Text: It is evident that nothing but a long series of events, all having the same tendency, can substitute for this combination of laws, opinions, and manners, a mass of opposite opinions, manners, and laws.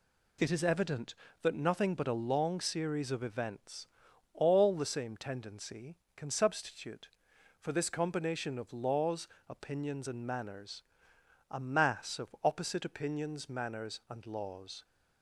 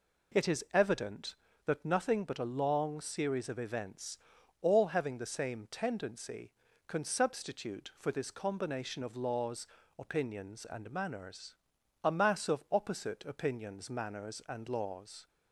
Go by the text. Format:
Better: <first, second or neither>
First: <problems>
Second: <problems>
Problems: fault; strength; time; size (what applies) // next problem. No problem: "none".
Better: second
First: skips "having"; at 4.7 s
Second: none